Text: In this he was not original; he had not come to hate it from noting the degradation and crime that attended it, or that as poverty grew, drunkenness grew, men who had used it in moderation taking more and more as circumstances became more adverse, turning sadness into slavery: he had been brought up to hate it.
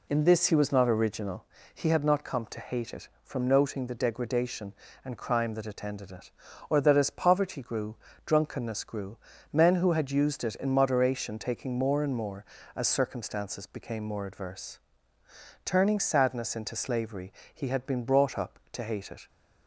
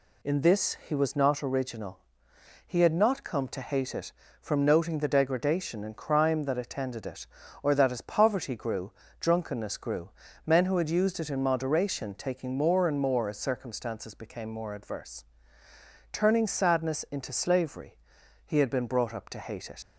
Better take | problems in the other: first | leaves "it" unfinished; at 19.8 s; 90 ms

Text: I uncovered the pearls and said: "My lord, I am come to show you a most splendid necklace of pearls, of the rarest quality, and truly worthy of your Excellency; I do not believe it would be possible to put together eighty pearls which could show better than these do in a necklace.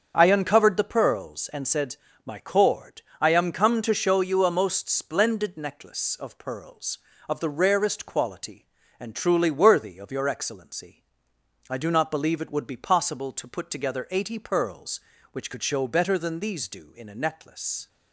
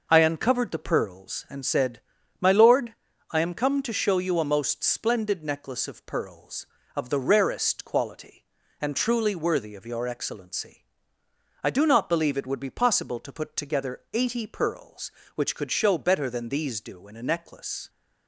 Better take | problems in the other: second | starts louder than the rest; until 1.1 s; 7 dB // says "cord" for "lord"; at 2.3 s

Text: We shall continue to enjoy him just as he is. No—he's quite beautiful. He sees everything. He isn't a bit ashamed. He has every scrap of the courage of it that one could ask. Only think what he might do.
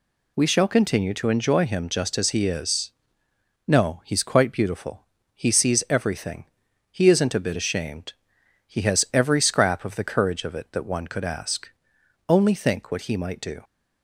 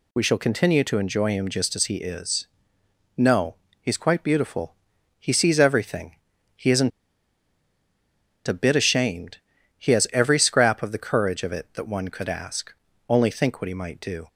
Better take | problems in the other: first | pauses between "isn't" and "a"; strong; at 6.9 s; 1.5 s long

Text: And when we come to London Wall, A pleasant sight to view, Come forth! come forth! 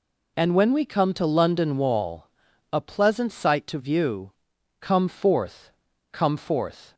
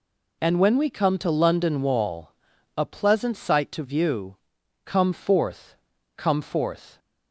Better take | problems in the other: neither | none

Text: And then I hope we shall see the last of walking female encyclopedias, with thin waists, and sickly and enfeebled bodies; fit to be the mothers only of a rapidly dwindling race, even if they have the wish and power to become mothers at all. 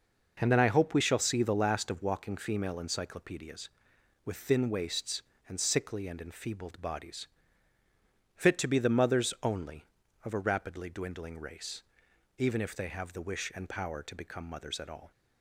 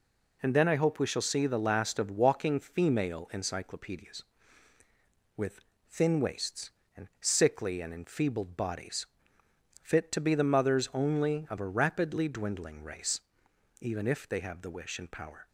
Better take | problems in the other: first | pauses between "with" and "thin"; slight; at 5.6 s; 0.30 s long // stops before "to become mothers at all"; at 15.4 s

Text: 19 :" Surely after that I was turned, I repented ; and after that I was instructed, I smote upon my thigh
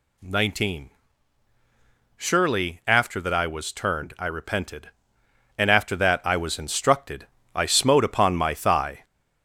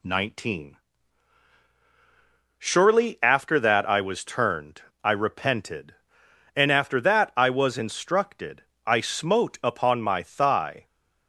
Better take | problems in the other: second | gets louder; strong; throughout; 17 dB

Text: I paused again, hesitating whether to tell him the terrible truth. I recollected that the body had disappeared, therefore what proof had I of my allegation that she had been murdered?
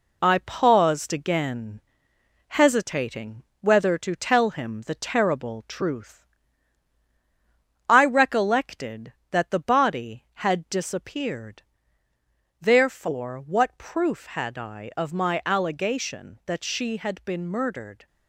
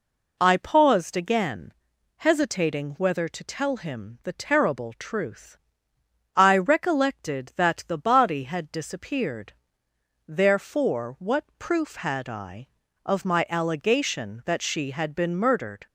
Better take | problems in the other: second | gets quieter; noticeable; throughout; 4.5 dB // pauses between "hesitating" and "whether"; slight; at 3.4 s; 0.18 s long

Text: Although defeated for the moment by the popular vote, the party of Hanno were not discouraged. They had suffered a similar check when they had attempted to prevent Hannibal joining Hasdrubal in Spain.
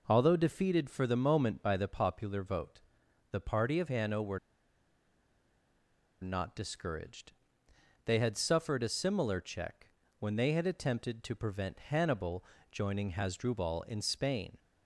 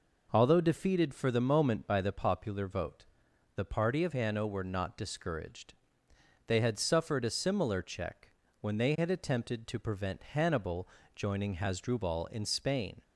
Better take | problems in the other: second | pauses between "were" and "not"; strong; at 4.3 s; 1.8 s long // pauses between "check" and "when"; slight; at 9.8 s; 0.30 s long; slight in the second // pauses between "Hannibal" and "joining"; slight; at 12.4 s; 0.26 s long; slight in the second

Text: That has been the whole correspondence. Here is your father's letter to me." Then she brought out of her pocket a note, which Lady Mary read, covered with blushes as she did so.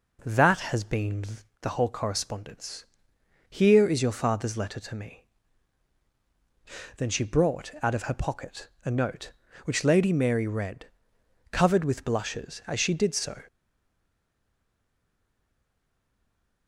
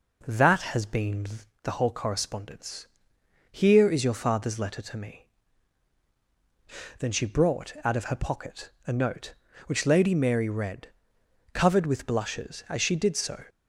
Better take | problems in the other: second | pauses between "been" and "the"; at 1.2 s; 0.38 s long; also in the second // pauses between "pocket" and "a"; slight; at 8.6 s; 0.16 s long; slight in the second // stays silent after the last word; strong; from 13.4 s on; 3.2 s long

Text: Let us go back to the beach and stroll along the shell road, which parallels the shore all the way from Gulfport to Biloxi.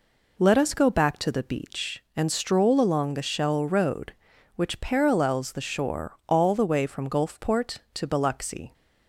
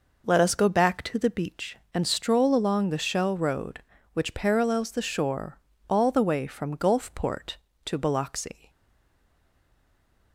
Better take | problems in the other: first | pauses between "shore" and "all"; slight; at 5.5 s; 0.28 s long // stays silent after the last word; noticeable; from 8.6 s on; 1.7 s long

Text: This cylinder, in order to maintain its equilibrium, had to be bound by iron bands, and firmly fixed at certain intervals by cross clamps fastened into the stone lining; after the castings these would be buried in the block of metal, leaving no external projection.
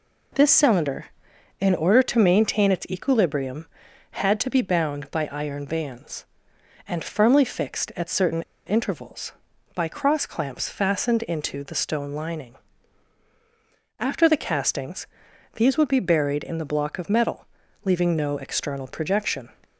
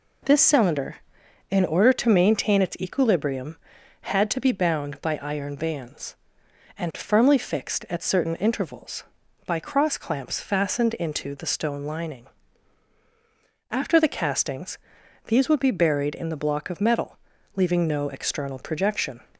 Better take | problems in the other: second | pauses between "certain" and "intervals"; slight; at 8.4 s; 0.24 s long // pauses between "castings" and "these"; noticeable; at 15.0 s; 0.48 s long; noticeable in the second

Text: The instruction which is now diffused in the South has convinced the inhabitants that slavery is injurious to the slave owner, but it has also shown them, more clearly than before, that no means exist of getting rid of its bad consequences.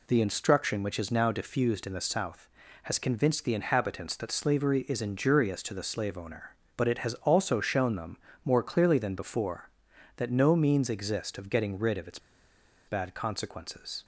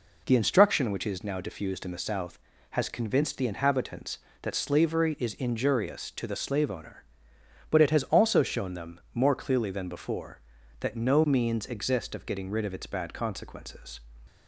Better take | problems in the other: second | pauses between "its" and "bad"; noticeable; at 12.1 s; 0.69 s long

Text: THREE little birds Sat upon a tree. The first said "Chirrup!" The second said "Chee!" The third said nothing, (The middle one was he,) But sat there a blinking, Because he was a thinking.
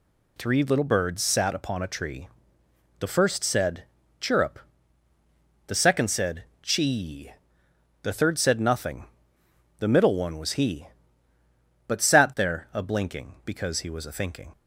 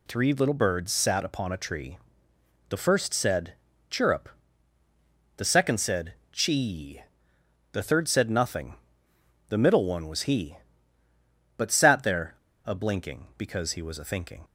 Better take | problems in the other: first | pauses between "said" and "Chirrup"; slight; at 3.5 s; 0.36 s long; slight in the first // pauses between "said" and "Chee"; slight; at 6.1 s; 0.18 s long; slight in the first // pauses between "there" and "a"; slight; at 12.3 s; 0.29 s long

